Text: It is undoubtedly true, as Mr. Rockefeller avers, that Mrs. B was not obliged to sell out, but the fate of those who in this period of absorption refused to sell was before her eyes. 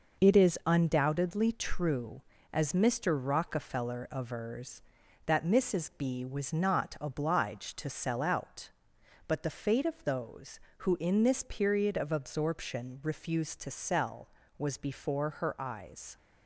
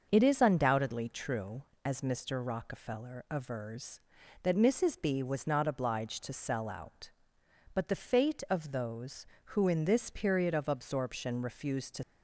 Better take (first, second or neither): first